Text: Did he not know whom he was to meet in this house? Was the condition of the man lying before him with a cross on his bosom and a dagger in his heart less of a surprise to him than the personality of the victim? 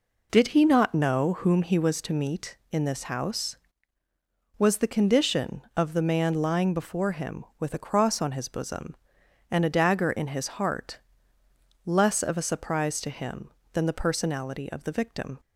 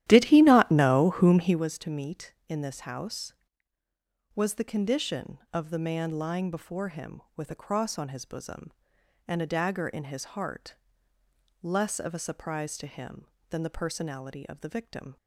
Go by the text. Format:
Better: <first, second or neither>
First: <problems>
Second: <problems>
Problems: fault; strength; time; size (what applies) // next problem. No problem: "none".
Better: first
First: pauses between "heart" and "less"; noticeable; at 10.9 s; 0.84 s long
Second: starts louder than the rest; strong; until 1.6 s; 13 dB // pauses between "heart" and "less"; noticeable; at 10.7 s; 0.84 s long